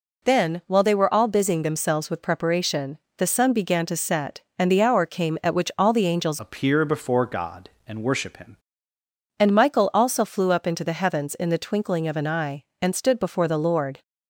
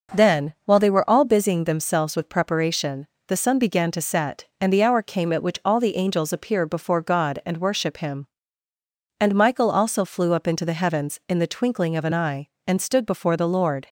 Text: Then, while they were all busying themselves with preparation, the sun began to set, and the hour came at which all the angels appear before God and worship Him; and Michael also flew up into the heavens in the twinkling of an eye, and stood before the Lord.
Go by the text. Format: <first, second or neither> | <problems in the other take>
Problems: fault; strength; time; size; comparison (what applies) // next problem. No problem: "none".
second | changes voice from "appear" to "Him"; from 6.3 to 8.5 s; 2.2 s long